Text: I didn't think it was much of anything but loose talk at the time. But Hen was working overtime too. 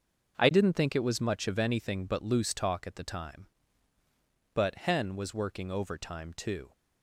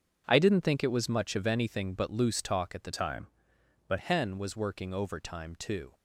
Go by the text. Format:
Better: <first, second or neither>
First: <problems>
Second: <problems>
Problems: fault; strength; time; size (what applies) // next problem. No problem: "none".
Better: first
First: starts louder than the rest; until 1.3 s; 6.5 dB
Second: starts louder than the rest; strong; until 1.2 s; 7 dB // changes voice from "time" to "But"; from 2.9 to 3.9 s; 1.0 s long